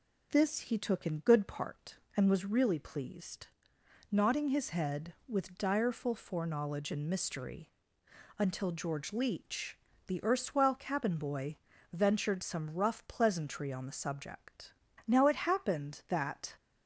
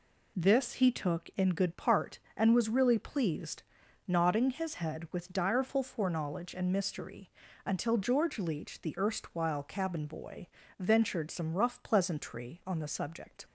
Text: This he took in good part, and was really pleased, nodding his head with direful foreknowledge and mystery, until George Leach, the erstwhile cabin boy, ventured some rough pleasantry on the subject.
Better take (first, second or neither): second